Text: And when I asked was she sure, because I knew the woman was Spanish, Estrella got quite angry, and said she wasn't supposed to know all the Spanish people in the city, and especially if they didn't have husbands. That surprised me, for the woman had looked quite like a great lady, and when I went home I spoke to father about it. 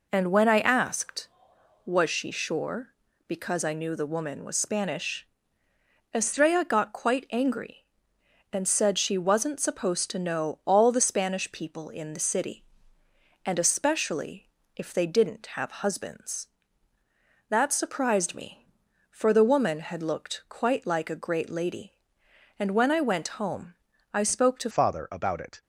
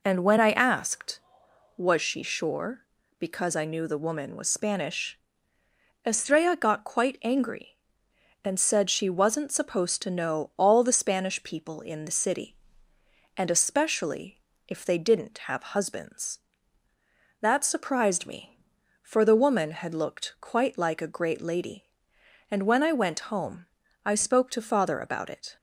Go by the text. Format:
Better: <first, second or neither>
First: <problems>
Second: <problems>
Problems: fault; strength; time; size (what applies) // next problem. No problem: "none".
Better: second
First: pauses between "especially" and "if"; slight; at 14.4 s; 0.28 s long // pauses between "home" and "I"; at 23.7 s; 0.38 s long // changes voice at "father"; from 24.6 s on; 1.0 s long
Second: pauses between "especially" and "if"; slight; at 14.4 s; 0.28 s long // pauses between "home" and "I"; at 23.6 s; 0.38 s long